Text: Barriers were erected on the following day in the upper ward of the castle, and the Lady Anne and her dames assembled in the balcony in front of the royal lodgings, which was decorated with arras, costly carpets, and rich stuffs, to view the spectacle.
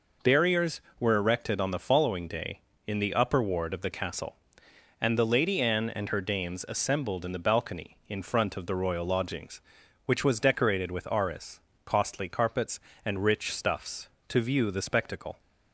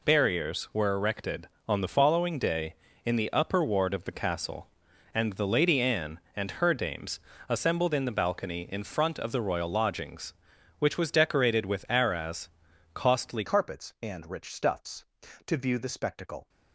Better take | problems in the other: first | pauses between "dames" and "assembled"; slight; at 7.1 s; 0.28 s long // changes voice at "carpets"; from 13.4 s on; 3.0 s long

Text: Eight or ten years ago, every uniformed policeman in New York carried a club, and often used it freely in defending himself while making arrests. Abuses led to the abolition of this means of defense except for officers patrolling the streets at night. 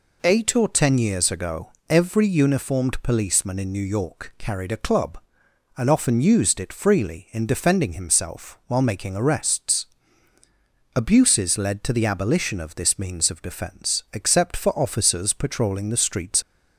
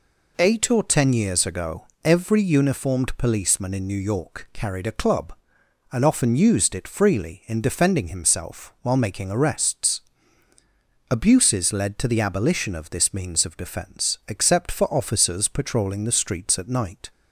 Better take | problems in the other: second | stops before "at night"; at 16.4 s

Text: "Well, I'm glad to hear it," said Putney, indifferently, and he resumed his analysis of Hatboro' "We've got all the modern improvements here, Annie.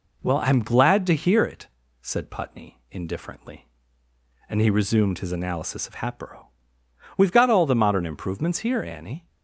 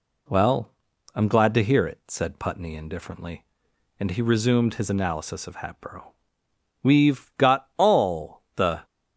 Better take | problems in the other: first | pauses between "Hatboro" and "We've"; noticeable; at 6.1 s; 0.76 s long; noticeable in the first // stops before "modern improvements here Annie"; at 8.8 s

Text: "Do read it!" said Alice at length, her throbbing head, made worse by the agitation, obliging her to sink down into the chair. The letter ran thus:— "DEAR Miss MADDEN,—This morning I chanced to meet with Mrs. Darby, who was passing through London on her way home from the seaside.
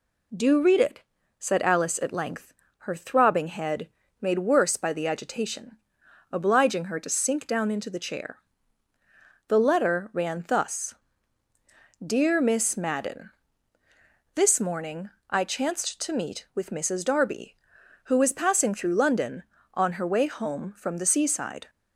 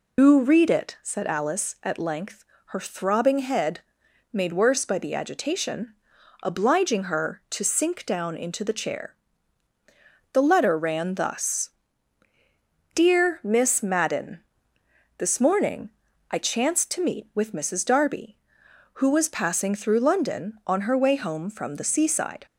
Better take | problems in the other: first | loses the start of "Do"; at 0.1 s; 125 ms // pauses between "morning" and "I"; at 15.8 s; 0.40 s long; slight in the first

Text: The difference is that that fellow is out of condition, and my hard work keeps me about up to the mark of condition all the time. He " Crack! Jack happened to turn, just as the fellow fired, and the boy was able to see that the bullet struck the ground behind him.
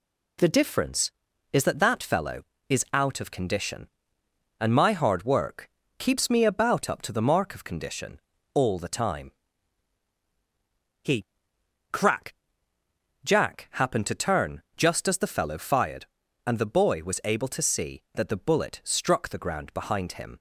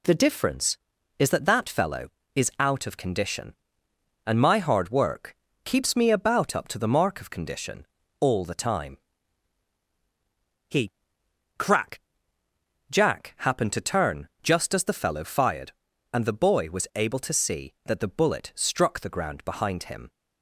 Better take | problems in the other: neither | pauses between "work" and "keeps"; slight; the same in both // pauses between "condition" and "all"; slight; the same in both

